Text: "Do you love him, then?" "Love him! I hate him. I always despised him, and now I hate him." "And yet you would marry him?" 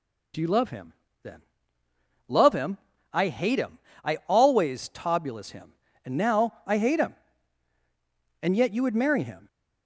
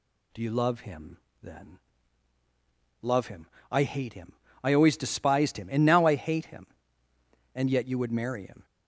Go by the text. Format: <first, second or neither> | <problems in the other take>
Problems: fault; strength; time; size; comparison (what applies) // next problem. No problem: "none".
second | says "tobulus" for "despised"; at 4.8 s